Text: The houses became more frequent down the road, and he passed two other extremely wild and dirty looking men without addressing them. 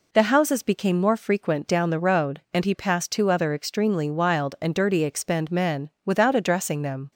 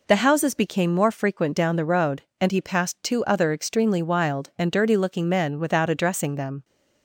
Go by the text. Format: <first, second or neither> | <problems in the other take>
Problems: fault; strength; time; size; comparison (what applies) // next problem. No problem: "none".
second | says "expend" for "looking"; at 5.0 s // pauses between "men" and "without"; slight; at 5.8 s; 0.16 s long